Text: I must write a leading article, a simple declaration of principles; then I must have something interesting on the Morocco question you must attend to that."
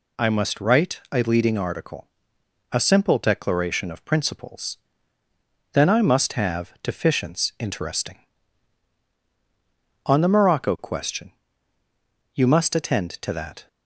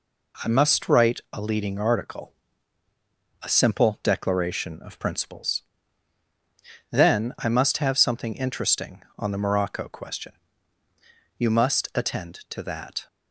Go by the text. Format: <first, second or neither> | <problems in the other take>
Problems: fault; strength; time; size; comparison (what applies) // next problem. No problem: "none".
second | says "deficients" for "something"; at 6.8 s // pauses between "question" and "you"; at 11.3 s; 1.0 s long; also in the second